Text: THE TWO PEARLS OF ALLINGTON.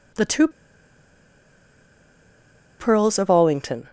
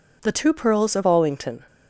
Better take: second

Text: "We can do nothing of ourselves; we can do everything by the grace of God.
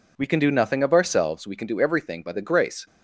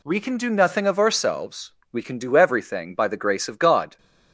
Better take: second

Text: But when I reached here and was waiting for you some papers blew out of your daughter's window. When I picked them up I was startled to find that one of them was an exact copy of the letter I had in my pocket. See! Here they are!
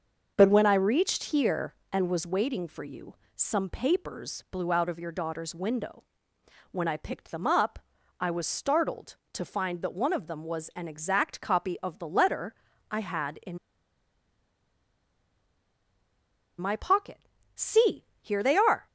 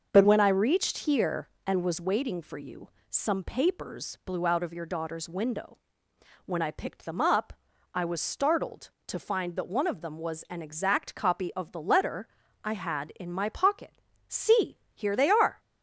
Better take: second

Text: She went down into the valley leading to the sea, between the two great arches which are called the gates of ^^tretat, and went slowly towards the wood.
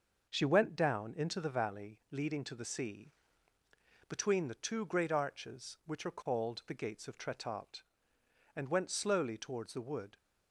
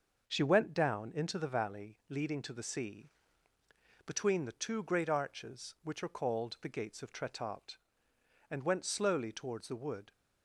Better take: neither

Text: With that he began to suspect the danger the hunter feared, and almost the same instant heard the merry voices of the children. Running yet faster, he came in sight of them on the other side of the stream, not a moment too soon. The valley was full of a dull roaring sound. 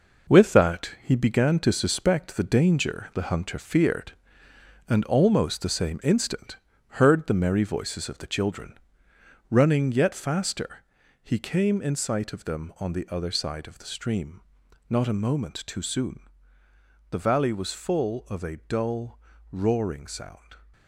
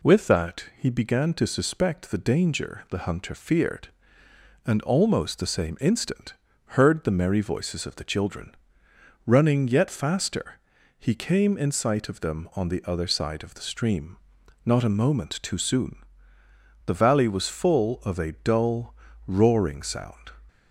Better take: second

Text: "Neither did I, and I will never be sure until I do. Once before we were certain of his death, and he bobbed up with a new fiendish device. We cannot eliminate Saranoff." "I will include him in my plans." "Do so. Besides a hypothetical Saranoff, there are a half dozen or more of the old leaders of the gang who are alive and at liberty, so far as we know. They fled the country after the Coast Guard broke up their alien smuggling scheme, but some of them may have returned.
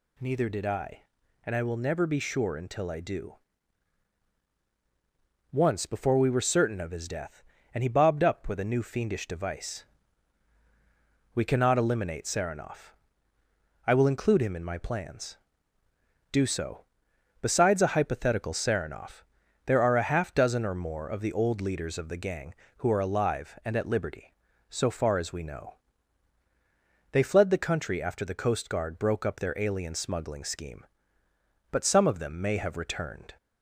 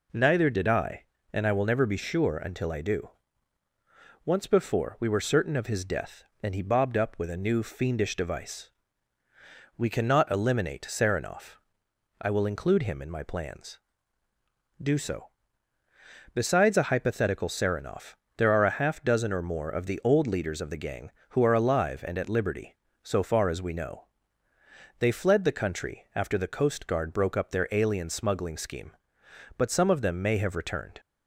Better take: neither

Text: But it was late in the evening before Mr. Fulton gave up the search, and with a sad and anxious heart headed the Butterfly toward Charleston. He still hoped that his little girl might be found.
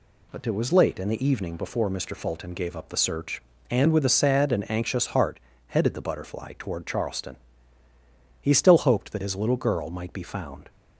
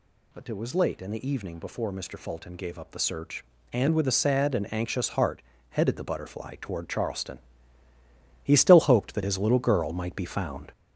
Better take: first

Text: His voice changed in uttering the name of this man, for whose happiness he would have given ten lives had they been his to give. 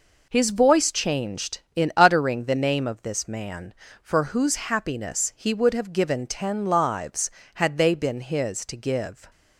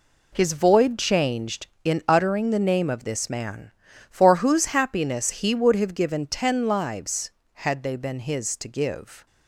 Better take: first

